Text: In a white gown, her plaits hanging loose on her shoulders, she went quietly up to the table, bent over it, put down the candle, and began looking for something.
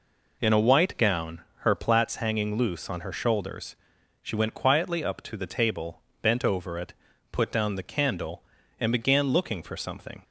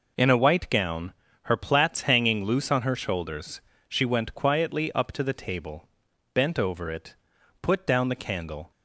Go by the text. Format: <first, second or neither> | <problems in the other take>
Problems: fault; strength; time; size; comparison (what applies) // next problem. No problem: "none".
first | stops before "and began looking for something"; at 8.7 s